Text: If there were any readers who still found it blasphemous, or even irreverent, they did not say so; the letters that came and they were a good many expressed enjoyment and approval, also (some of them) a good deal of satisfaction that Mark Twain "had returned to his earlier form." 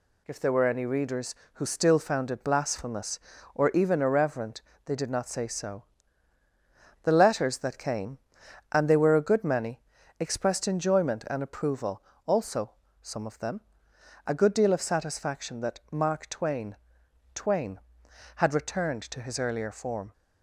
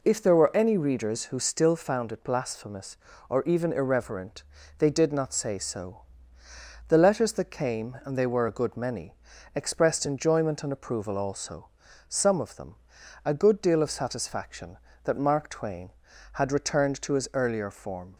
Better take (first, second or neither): second